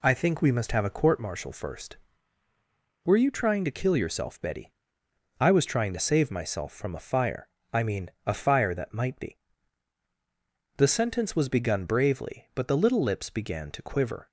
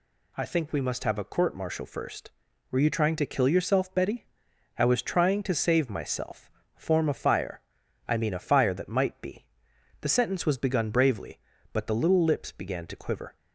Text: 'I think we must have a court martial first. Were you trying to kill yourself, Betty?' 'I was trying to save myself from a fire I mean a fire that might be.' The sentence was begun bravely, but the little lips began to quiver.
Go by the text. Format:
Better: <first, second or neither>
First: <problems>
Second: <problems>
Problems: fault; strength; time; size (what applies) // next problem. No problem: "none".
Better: first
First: pauses between "fire" and "I"; slight; at 7.4 s; 0.26 s long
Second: says "form" for "from"; at 6.7 s // pauses between "fire" and "I"; noticeable; at 7.6 s; 0.48 s long